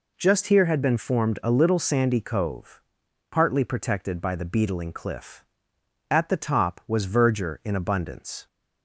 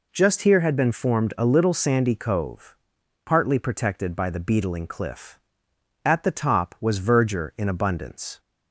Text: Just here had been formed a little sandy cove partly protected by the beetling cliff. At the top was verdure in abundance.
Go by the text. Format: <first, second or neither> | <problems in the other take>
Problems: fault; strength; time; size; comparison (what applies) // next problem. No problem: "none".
neither | pauses between "cove" and "partly"; noticeable; the same in both